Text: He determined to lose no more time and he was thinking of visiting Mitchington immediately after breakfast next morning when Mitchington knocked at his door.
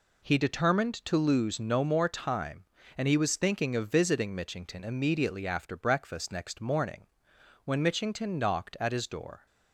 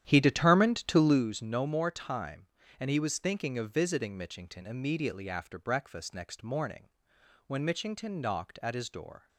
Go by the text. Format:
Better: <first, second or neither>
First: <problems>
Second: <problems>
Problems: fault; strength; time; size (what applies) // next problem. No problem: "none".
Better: first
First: pauses between "morning" and "when"; noticeable; at 7.0 s; 0.60 s long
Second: starts louder than the rest; strong; until 1.2 s; 10.5 dB // pauses between "morning" and "when"; noticeable; at 6.8 s; 0.60 s long